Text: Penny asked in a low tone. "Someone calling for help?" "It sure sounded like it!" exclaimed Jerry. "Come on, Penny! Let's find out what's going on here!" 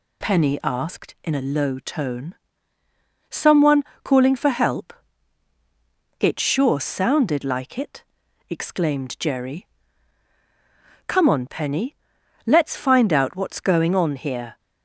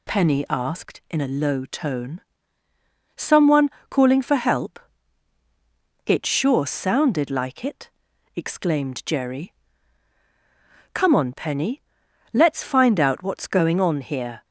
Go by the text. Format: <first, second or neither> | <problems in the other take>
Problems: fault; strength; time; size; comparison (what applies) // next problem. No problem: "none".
neither | pauses between "Someone" and "calling"; slight; the same in both